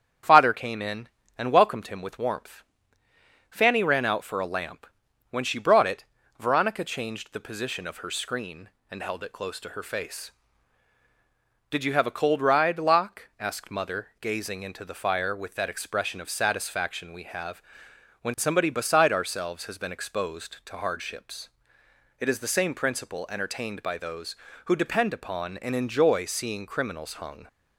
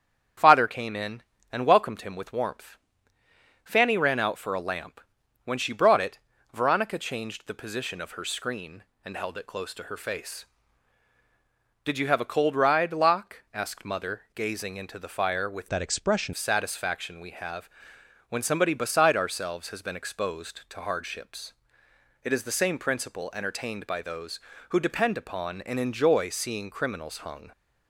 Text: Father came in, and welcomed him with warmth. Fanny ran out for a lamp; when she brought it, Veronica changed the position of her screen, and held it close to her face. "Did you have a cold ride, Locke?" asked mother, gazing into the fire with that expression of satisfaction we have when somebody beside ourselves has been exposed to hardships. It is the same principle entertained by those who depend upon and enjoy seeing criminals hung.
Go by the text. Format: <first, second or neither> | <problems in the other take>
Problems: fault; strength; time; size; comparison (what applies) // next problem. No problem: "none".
first | starts louder than the rest; strong; until 1.6 s; 8 dB; strong in the first // changes voice from "that" to "expression"; from 15.6 to 16.3 s; 0.7 s long // pauses between "have" and "when"; noticeable; at 17.6 s; 0.62 s long; noticeable in the first